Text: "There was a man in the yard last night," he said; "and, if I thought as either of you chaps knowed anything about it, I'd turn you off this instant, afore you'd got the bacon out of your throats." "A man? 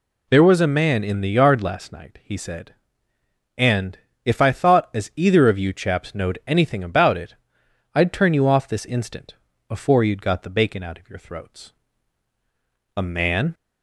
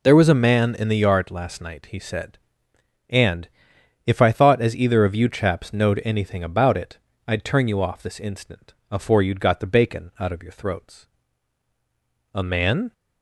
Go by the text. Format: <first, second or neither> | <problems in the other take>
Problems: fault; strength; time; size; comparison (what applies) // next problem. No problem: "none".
neither | none